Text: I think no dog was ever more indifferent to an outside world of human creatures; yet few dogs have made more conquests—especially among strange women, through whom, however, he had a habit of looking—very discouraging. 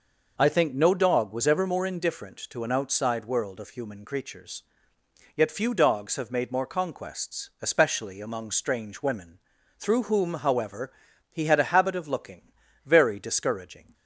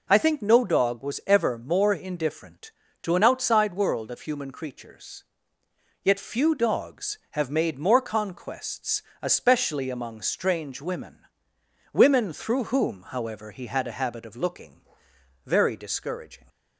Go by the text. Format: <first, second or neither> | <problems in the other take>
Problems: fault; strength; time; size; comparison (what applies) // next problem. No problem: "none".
first | says "women" twice; at 11.9 s